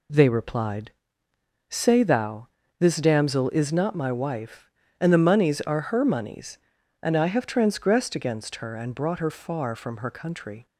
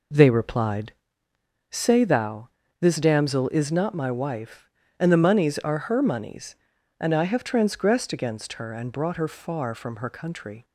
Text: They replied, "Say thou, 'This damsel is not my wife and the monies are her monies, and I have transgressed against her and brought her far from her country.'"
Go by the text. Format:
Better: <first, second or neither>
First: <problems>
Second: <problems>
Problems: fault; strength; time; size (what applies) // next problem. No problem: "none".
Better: first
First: none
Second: starts louder than the rest; noticeable; until 1.2 s; 4 dB